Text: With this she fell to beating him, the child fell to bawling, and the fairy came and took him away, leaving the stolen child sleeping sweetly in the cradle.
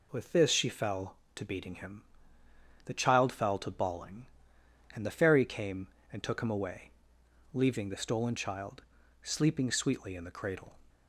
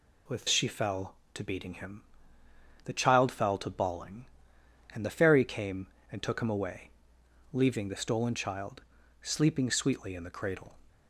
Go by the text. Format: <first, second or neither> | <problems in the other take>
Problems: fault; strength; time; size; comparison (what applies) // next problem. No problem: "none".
first | skips "this"; at 0.4 s // pauses between "child" and "sleeping"; at 8.8 s; 0.40 s long; also in the first